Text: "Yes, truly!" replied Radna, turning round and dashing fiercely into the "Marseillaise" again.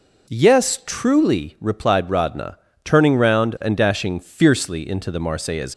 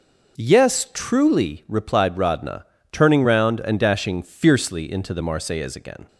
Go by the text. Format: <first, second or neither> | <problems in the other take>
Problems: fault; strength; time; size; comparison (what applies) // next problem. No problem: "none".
second | stops before "again"; at 5.7 s